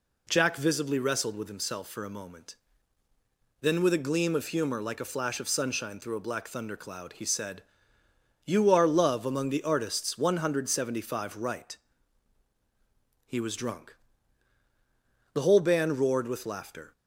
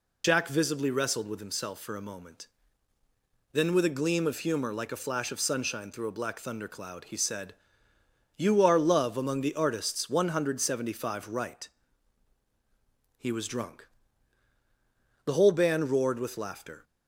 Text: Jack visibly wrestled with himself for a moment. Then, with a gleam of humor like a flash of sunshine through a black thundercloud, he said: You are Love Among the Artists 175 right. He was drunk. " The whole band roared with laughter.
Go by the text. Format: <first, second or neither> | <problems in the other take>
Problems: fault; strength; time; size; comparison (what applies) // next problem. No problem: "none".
first | loses the start of "Jack"; at 0.2 s; 50 ms